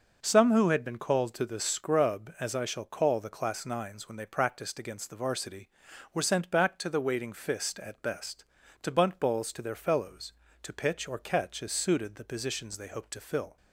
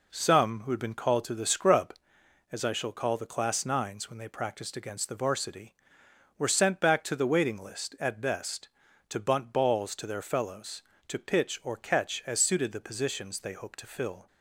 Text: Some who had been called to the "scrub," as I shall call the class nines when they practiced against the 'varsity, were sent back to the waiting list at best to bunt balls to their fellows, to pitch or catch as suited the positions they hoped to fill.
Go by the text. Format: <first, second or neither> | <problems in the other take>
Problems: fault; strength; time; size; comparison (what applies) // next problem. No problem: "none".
second | says "fist" for "list"; at 7.3 s